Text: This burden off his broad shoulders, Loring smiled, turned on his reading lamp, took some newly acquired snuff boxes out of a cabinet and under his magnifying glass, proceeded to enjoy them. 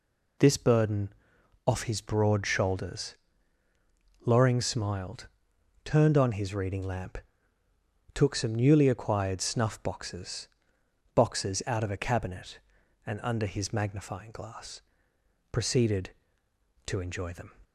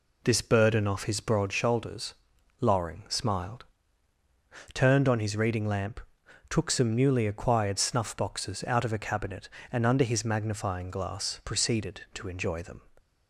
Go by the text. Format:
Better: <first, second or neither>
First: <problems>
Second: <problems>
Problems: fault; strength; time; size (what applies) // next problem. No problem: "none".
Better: second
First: pauses between "burden" and "off"; noticeable; at 1.1 s; 0.54 s long // says "boxes" twice; at 11.1 s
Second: none